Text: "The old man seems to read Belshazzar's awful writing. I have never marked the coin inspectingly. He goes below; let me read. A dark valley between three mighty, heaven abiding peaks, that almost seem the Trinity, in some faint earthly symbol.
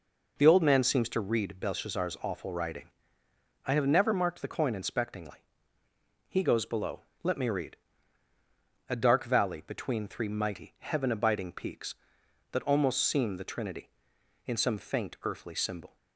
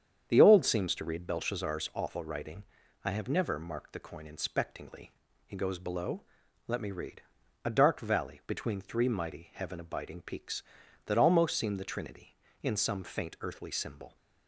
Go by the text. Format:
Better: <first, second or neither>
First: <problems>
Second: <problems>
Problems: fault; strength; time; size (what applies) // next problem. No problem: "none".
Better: first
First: none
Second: starts louder than the rest; strong; until 1.3 s; 8 dB // skips "man"; at 0.6 s